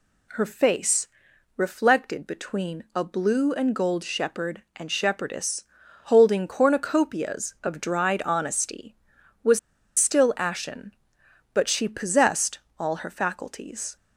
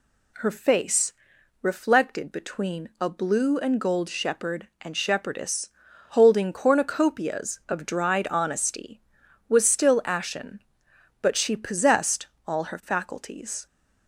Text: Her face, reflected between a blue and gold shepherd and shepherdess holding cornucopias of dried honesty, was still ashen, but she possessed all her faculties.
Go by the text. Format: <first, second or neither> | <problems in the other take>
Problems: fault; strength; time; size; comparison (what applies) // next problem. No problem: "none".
second | pauses between "shepherdess" and "holding"; at 5.6 s; 0.40 s long; also in the second // pauses between "was" and "still"; at 9.5 s; 0.40 s long // pauses between "possessed" and "all"; slight; at 12.5 s; 0.18 s long; slight in the second